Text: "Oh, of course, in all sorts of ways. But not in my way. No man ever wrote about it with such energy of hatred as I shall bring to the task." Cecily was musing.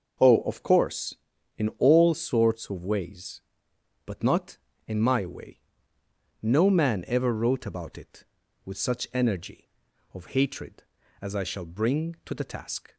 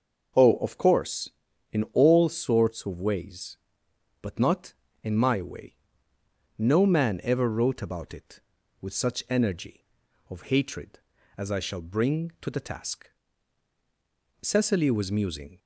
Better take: second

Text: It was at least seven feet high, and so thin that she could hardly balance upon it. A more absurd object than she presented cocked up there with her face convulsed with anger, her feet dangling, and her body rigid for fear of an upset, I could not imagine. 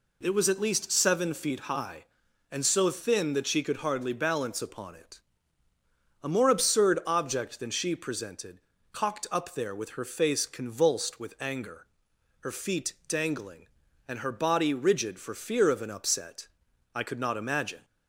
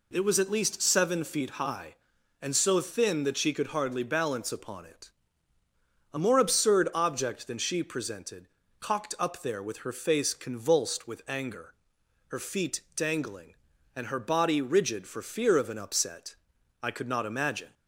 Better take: neither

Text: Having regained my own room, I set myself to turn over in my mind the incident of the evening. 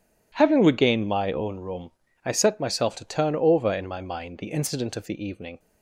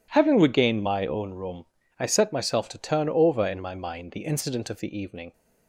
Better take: neither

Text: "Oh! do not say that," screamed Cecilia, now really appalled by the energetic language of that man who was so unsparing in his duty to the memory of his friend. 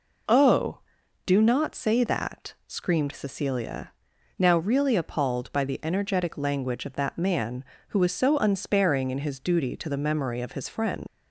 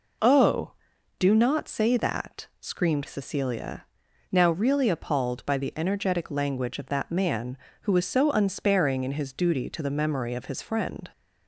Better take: second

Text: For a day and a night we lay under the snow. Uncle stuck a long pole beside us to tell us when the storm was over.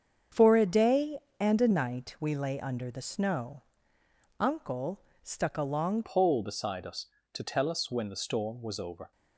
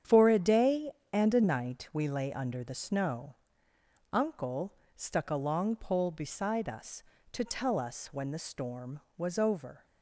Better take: second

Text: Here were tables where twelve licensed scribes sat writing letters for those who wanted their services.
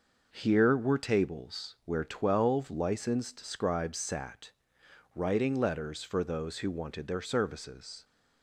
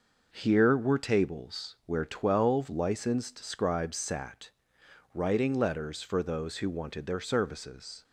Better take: neither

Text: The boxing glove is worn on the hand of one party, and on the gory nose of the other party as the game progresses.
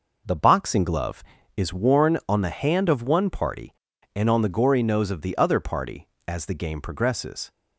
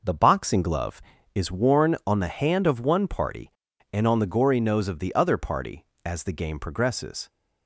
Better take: neither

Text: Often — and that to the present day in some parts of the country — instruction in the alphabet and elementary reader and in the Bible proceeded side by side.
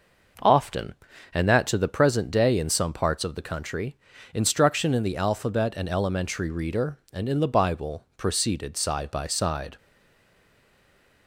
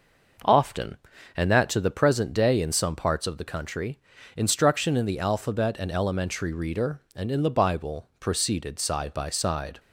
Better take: second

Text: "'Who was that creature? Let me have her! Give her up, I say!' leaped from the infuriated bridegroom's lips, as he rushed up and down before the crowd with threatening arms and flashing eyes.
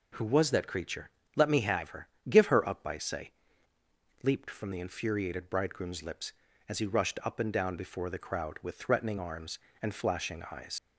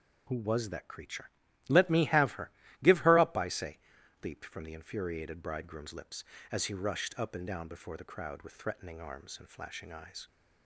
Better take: second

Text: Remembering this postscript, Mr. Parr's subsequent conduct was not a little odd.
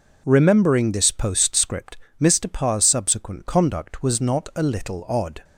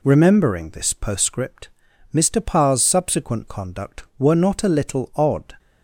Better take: first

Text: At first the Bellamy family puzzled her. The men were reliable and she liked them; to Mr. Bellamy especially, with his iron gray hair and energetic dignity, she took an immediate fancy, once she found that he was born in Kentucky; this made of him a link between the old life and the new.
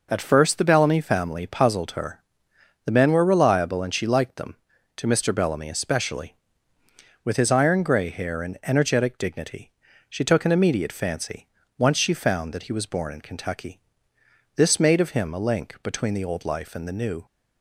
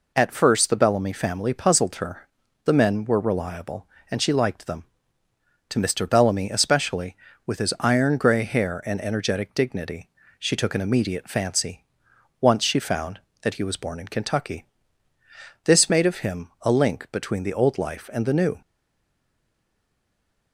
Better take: first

